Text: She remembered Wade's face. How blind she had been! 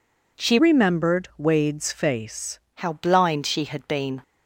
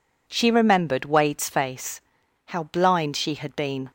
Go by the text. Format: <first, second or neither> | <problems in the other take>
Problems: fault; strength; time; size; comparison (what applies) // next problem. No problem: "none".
second | changes voice from "remembered" to "face"; from 0.5 to 2.5 s; 2.0 s long